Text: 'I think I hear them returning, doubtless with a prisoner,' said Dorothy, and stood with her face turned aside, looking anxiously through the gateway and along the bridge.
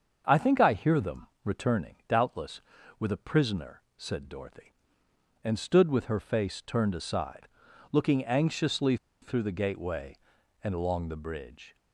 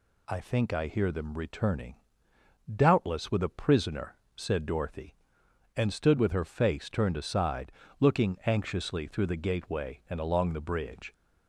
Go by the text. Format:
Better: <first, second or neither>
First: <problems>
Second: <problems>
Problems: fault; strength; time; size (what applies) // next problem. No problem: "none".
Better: second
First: starts louder than the rest; until 1.4 s; 6.5 dB // pauses between "them" and "returning"; slight; at 1.2 s; 0.16 s long // pauses between "anxiously" and "through"; slight; at 8.9 s; 0.26 s long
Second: none